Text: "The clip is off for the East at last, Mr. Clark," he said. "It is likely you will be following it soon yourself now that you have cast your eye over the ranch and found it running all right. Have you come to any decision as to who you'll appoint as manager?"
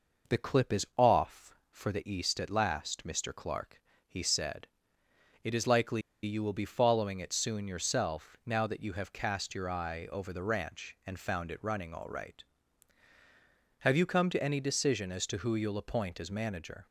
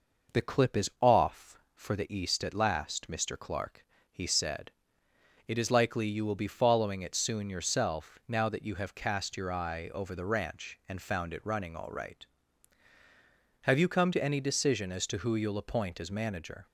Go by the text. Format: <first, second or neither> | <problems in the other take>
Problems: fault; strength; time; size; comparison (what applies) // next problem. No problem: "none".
second | pauses between "likely" and "you"; slight; at 6.0 s; 0.22 s long